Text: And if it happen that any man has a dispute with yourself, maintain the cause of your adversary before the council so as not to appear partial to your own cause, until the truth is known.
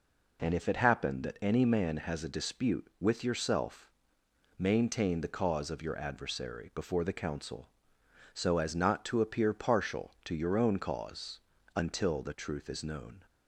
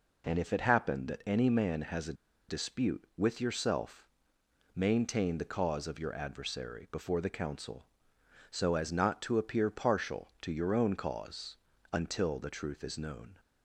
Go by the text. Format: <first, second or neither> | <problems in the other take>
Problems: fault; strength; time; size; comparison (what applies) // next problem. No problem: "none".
first | pauses between "a" and "dispute"; slight; at 2.1 s; 0.35 s long